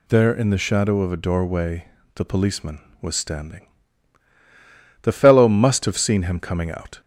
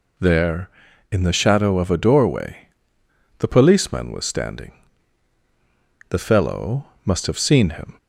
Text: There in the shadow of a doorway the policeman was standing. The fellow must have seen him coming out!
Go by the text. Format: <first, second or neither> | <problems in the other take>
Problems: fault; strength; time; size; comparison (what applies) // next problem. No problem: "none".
first | pauses between "doorway" and "the"; noticeable; at 2.6 s; 0.70 s long; slight in the first // pauses between "fellow" and "must"; slight; at 6.8 s; 0.18 s long // stops before "coming out"; at 7.9 s